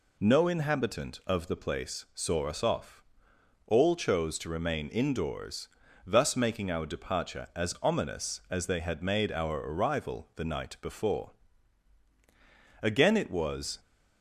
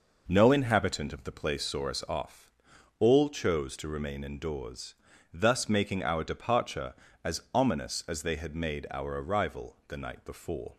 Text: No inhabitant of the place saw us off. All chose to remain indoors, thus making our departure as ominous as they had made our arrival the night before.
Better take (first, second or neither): second